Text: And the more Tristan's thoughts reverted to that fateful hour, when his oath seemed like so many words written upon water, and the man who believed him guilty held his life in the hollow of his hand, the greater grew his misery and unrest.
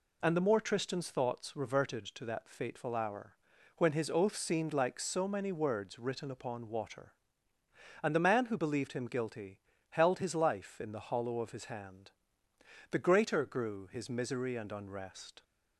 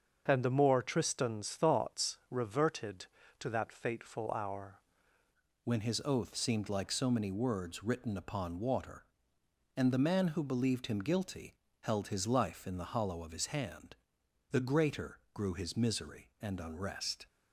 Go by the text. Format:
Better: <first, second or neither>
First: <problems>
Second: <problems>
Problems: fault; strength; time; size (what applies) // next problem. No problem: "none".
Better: first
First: pauses between "guilty" and "held"; slight; at 9.5 s; 0.32 s long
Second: starts louder than the rest; until 1.2 s; 6.5 dB // changes voice at "when"; from 5.6 s on; 11.6 s long // pauses between "guilty" and "held"; slight; at 11.5 s; 0.28 s long